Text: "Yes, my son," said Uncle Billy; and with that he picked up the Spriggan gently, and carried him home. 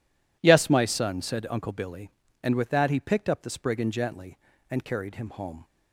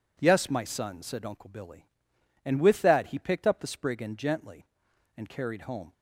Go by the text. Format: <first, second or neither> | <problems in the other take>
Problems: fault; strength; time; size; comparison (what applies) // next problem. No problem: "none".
first | skips "him"; at 5.6 s